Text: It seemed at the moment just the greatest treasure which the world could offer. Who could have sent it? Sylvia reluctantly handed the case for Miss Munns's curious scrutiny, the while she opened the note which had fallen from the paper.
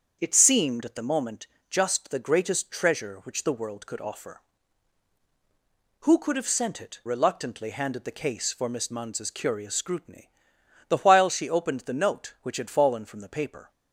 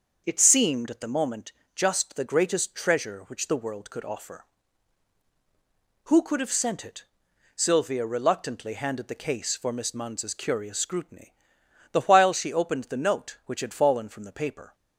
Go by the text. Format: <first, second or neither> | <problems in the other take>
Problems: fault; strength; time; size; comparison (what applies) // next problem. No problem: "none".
second | starts louder than the rest; strong; until 1.2 s; 7 dB; also in the second // pauses between "moment" and "just"; slight; at 1.4 s; 0.22 s long; slight in the second // skips "Sylvia"; at 7.0 s